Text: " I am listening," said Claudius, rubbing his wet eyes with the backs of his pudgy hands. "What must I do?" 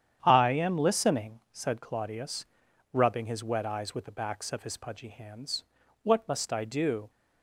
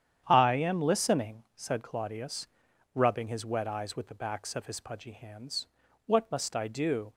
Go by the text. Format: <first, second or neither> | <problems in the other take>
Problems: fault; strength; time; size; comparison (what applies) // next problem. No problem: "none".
neither | starts louder than the rest; strong; the same in both